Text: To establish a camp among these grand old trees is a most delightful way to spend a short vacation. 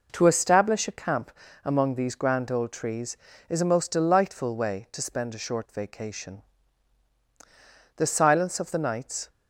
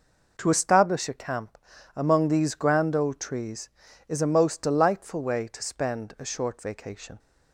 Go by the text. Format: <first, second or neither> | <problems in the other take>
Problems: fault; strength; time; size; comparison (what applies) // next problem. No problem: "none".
second | pauses between "camp" and "among"; slight; at 1.3 s; 0.32 s long; also in the second // goes on to say "The silence of the nights"; from 7.9 s on; 1.3 s long